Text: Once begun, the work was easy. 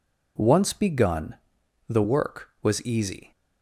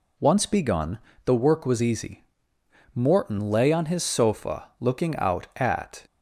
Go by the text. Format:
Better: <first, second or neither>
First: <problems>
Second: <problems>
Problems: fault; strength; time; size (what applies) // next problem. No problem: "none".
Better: first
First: none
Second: goes on to say "Morton lay on his sofa looking out at"; strong; from 2.9 s on; 3.0 s long